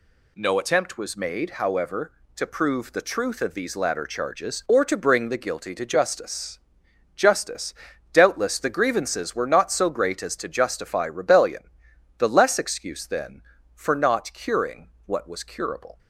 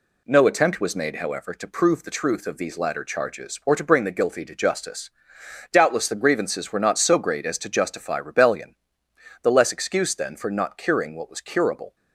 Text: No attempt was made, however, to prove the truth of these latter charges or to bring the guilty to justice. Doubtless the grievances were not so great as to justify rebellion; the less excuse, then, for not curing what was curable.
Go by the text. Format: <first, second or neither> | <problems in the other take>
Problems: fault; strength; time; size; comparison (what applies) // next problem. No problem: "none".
second | says "justice" twice; at 7.1 s // pauses between "curing" and "what"; slight; at 14.8 s; 0.18 s long